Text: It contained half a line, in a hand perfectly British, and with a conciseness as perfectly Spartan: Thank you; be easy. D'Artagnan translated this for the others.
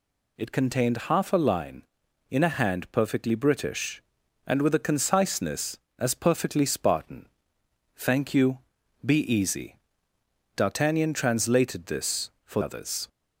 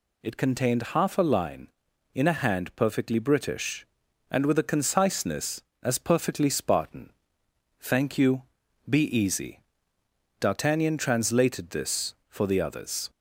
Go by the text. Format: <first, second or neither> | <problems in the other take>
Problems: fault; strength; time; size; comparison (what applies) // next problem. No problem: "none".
second | skips "the"; at 12.6 s